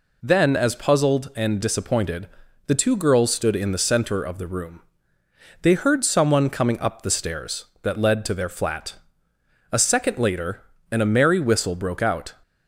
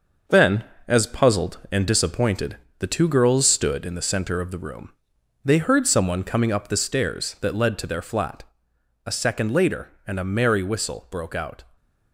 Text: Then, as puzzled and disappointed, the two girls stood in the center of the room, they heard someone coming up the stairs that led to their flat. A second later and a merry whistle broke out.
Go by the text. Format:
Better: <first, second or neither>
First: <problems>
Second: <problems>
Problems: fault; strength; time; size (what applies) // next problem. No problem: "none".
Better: first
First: none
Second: gets quieter; noticeable; throughout; 5.5 dB